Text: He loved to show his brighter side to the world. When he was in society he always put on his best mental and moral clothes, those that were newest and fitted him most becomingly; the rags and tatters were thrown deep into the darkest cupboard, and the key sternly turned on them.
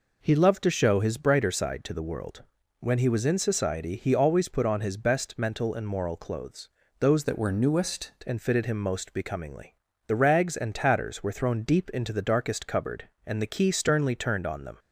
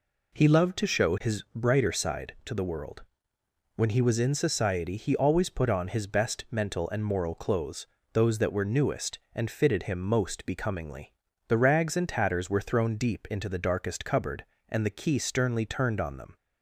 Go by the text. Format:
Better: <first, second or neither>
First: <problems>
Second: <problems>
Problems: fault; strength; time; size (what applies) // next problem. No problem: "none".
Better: second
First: changes voice from "that" to "newest"; from 7.2 to 8.1 s; 0.9 s long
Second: none